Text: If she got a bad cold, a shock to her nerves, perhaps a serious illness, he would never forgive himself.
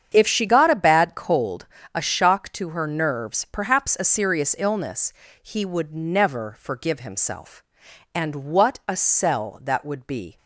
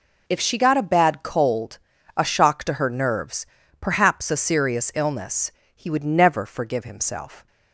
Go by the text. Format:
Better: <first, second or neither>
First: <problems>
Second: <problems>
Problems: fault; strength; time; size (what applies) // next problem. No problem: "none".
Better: second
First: starts louder than the rest; strong; until 1.1 s; 8 dB // goes on to say "And what a sell that would be"; strong; from 8.1 s on; 2.2 s long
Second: none